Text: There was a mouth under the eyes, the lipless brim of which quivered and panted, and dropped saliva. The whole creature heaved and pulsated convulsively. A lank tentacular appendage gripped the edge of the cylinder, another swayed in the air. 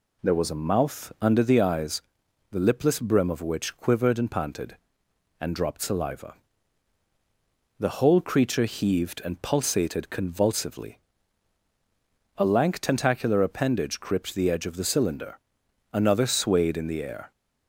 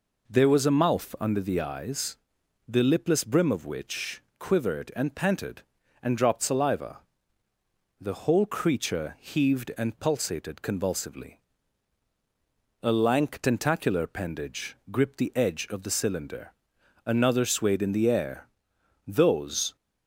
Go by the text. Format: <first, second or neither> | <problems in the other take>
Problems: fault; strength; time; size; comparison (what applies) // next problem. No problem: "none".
first | pauses between "which" and "quivered"; slight; at 4.2 s; 0.18 s long // pauses between "appendage" and "gripped"; slight; at 14.7 s; 0.16 s long // goes on to say "Those"; noticeable; from 19.0 s on; 0.70 s long